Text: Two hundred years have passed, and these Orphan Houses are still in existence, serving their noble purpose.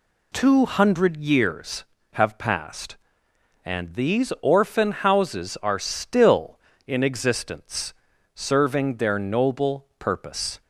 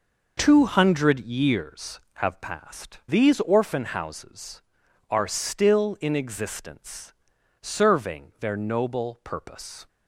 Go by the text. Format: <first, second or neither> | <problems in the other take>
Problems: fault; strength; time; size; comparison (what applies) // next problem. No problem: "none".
first | skips "and"; at 3.0 s